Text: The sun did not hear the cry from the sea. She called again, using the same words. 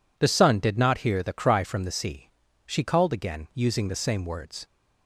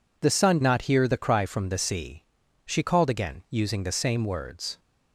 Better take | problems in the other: first | skips "did"; at 0.6 s

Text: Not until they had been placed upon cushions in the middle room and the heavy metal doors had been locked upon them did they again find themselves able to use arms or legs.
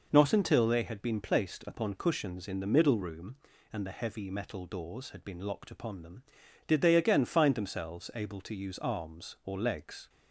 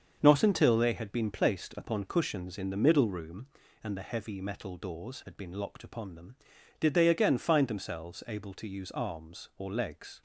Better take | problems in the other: first | gets quieter; strong; throughout; 7.5 dB

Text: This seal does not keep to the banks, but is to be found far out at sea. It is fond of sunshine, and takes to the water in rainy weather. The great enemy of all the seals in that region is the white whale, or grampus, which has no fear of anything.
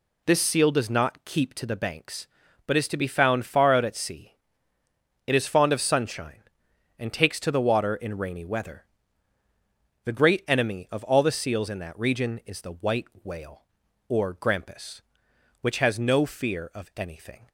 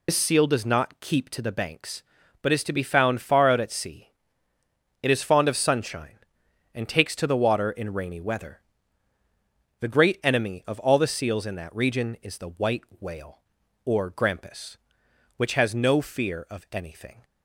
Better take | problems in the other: first | loses the start of "This"; at 0.0 s; 80 ms // pauses between "white" and "whale"; slight; at 12.8 s; 0.16 s long; slight in the first

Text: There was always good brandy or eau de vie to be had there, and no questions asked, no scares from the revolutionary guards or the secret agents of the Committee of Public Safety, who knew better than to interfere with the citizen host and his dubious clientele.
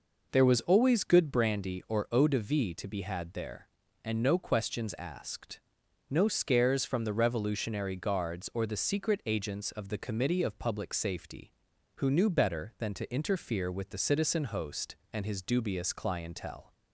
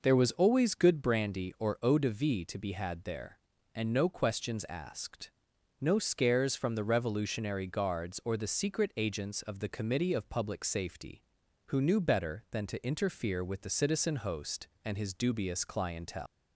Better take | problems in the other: first | leaves "clientele" unfinished; at 16.2 s; 195 ms

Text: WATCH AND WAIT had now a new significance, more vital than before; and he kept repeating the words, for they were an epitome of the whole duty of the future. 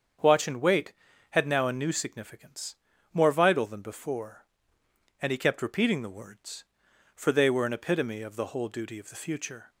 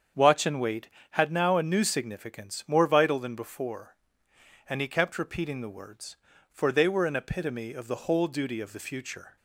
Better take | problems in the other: neither | starts louder than the rest; strong; the same in both

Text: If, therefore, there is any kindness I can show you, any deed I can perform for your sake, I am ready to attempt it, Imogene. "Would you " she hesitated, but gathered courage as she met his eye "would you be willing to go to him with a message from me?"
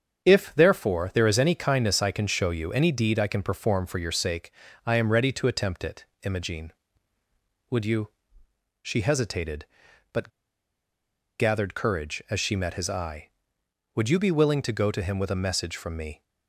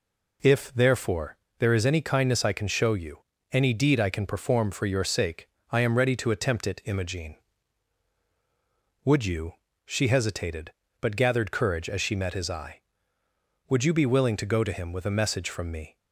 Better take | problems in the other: second | starts louder than the rest; strong; until 1.2 s; 8 dB // pauses between "but" and "gathered"; at 10.2 s; 1.1 s long

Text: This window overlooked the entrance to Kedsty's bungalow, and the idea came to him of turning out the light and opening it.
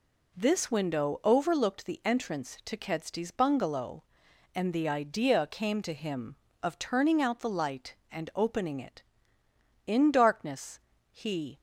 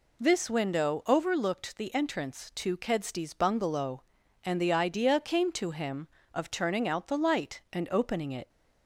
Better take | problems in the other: second | goes on to say "In darkness he"; strong; from 9.8 s on; 1.7 s long

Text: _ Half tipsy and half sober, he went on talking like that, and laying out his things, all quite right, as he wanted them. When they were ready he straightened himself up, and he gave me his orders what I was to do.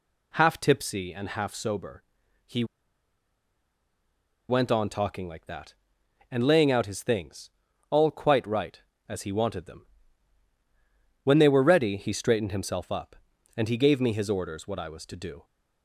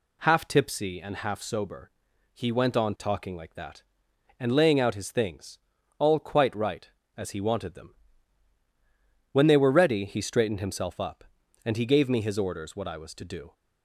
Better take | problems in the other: second | pauses between "he" and "went"; strong; at 2.6 s; 1.8 s long

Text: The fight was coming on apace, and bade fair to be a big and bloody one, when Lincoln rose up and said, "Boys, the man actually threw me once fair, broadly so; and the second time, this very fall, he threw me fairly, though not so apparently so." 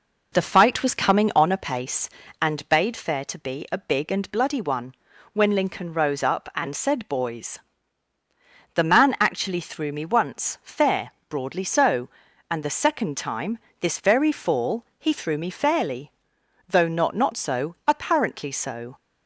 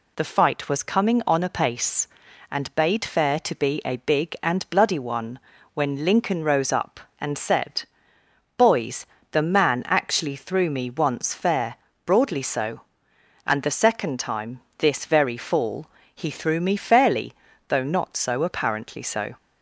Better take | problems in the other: second | says "not" twice; at 17.1 s

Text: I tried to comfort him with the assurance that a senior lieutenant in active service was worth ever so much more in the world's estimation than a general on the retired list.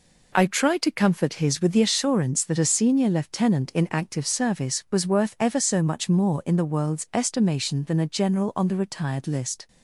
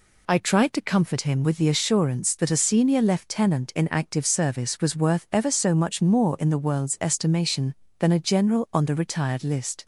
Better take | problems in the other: second | says "his" for "him"; at 1.3 s

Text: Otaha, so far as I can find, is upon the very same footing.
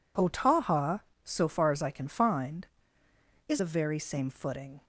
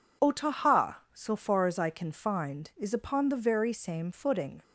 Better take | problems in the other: second | skips "upon"; at 3.5 s

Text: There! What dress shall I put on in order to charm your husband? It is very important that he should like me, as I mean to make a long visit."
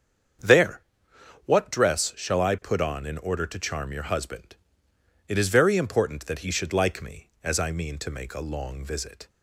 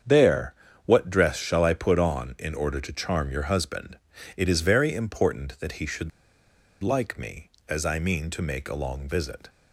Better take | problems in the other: first | starts louder than the rest; strong; until 1.3 s; 7.5 dB; strong in the first // pauses between "should" and "like"; noticeable; at 6.1 s; 0.71 s long

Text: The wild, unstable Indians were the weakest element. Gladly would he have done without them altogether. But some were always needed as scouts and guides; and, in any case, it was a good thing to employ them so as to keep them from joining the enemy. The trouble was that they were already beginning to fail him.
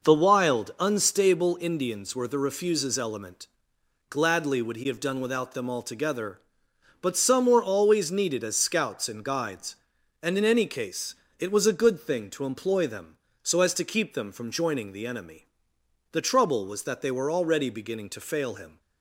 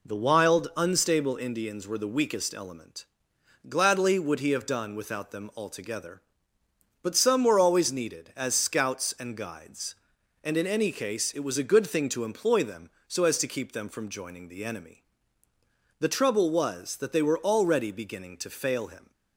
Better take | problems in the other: second | says "refuses" for "weakest"; at 2.3 s

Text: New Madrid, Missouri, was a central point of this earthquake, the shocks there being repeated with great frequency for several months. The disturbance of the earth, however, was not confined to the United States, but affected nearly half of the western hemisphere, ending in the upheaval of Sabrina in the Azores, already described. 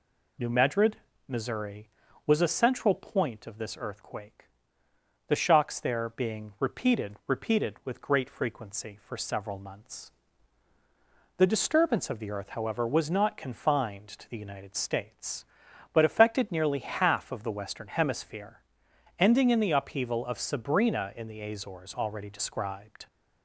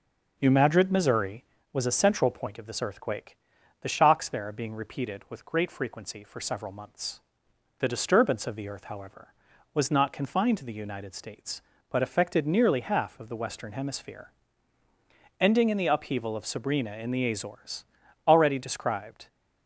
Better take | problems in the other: second | says "repeated" twice; at 7.2 s

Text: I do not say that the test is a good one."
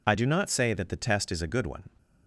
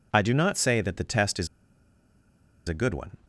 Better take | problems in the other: first | pauses between "is" and "a"; at 1.4 s; 1.2 s long

